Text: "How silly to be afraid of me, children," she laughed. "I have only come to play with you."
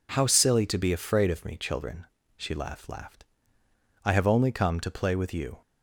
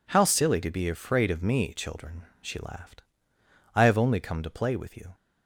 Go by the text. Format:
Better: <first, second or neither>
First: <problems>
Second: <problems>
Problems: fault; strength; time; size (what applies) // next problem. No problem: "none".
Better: second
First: says "laughed" twice; at 2.8 s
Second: none